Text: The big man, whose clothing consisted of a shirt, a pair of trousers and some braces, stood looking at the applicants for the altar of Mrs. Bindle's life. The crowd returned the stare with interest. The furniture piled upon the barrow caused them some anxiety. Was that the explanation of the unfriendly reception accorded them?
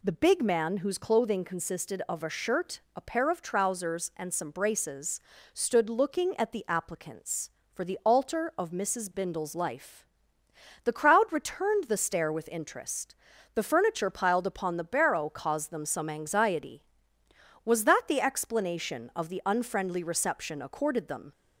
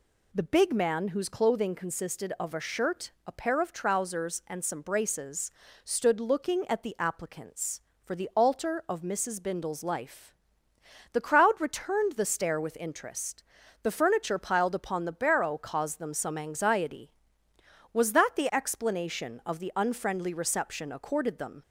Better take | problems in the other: neither | none

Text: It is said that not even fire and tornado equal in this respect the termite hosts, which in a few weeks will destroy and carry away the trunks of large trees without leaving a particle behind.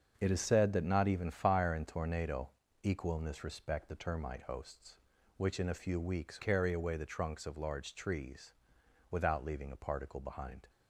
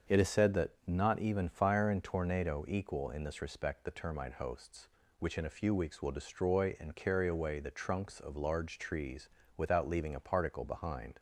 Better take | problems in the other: second | starts louder than the rest; until 1.1 s; 7 dB; also in the second // pauses between "tornado" and "equal"; slight; at 2.4 s; 0.34 s long // skips "will destroy and"; at 6.4 s // pauses between "trees" and "without"; noticeable; at 8.5 s; 0.60 s long; slight in the second

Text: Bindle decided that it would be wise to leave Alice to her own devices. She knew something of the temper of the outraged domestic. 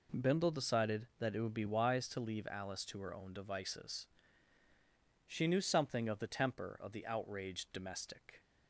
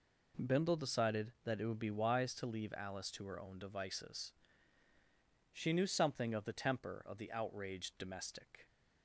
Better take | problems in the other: neither | none

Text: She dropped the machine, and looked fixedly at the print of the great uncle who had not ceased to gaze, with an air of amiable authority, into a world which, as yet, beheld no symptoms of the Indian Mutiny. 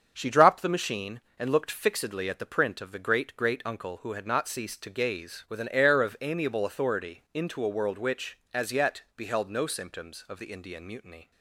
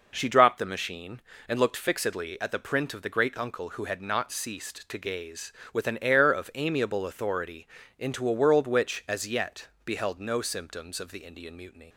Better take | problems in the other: second | starts louder than the rest; until 1.1 s; 6.5 dB // says "great" twice; at 3.3 s

